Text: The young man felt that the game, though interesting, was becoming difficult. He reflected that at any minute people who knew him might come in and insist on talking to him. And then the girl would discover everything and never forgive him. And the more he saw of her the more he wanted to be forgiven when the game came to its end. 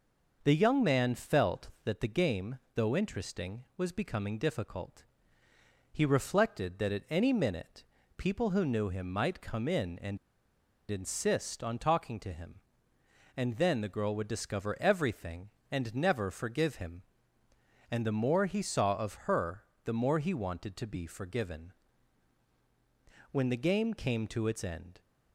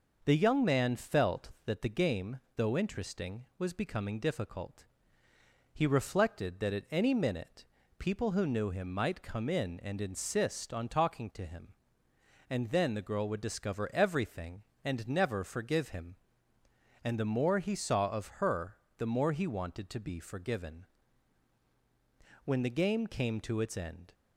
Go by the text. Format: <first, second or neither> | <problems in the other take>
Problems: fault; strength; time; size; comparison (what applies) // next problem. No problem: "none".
second | pauses between "minute" and "people"; slight; at 7.8 s; 0.34 s long; slight in the second // pauses between "and" and "insist"; noticeable; at 10.1 s; 0.72 s long // pauses between "her" and "the"; slight; at 19.6 s; 0.20 s long; slight in the second // pauses between "forgiven" and "when"; strong; at 21.7 s; 1.6 s long; strong in the second